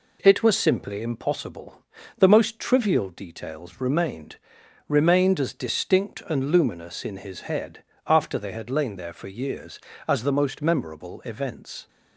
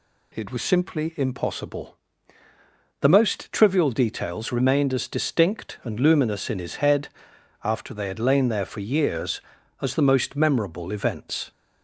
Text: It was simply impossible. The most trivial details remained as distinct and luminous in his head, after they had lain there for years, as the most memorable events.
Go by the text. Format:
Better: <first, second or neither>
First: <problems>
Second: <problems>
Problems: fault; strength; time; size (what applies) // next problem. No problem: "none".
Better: second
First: says "remained" twice; at 4.8 s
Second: none